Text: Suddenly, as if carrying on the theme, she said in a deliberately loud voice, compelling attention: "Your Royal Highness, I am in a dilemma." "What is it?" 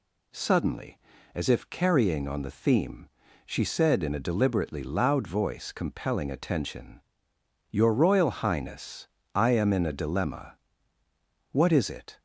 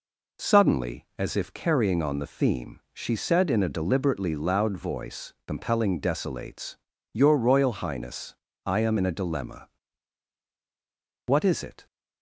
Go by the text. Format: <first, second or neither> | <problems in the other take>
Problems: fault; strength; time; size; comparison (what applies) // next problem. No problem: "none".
first | says "desolates" for "attention"; at 5.9 s